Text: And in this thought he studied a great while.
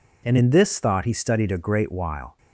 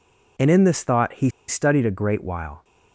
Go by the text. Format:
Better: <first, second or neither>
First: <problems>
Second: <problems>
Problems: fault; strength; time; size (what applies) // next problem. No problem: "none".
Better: first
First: none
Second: pauses between "he" and "studied"; slight; at 1.2 s; 0.19 s long